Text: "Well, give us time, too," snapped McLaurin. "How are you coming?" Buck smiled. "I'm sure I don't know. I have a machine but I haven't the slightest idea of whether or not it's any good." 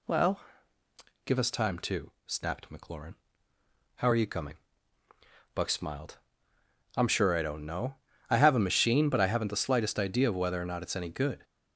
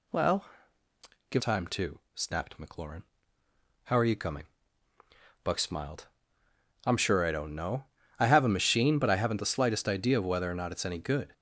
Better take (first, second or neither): first